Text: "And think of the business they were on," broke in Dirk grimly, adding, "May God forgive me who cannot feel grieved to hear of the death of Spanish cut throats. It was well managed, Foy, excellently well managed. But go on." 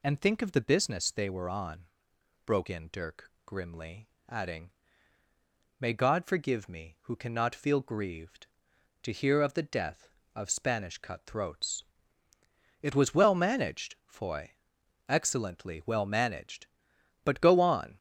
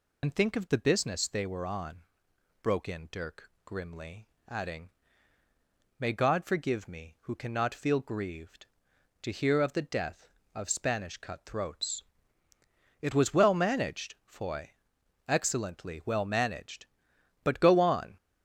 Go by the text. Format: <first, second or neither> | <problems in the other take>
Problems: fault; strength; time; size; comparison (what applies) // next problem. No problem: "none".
first | loses the start of "And"; at 0.2 s; 50 ms